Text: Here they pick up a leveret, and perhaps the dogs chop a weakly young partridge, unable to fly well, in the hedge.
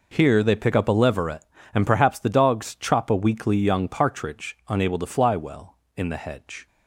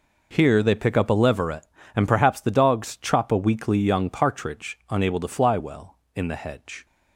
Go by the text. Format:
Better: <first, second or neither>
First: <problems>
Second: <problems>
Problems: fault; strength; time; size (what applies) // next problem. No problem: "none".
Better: neither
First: none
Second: none